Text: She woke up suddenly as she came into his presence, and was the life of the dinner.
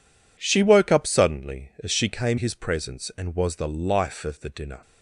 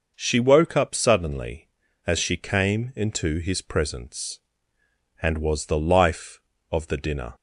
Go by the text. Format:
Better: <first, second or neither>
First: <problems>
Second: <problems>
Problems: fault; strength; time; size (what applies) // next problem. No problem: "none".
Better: second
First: skips "into"; at 2.3 s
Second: none